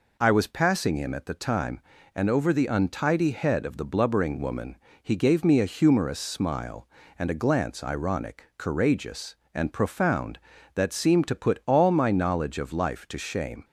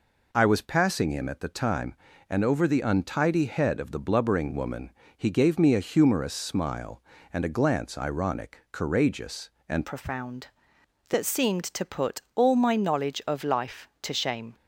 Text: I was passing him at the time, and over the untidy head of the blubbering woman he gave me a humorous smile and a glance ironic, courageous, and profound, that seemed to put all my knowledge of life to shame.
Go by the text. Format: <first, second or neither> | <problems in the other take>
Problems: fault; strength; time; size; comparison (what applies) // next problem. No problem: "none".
first | pauses between "woman" and "he"; slight; at 4.9 s; 0.24 s long; slight in the first // changes voice at "profound"; from 9.8 s on; 4.7 s long